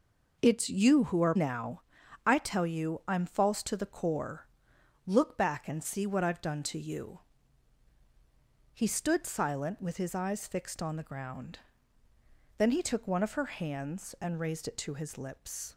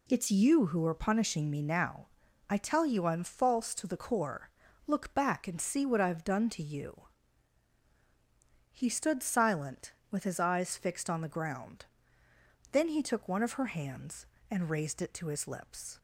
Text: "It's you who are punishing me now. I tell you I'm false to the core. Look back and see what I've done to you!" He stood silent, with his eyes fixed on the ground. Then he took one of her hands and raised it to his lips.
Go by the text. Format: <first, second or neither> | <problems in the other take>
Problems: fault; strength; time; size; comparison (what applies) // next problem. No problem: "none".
second | skips "punishing me"; at 1.3 s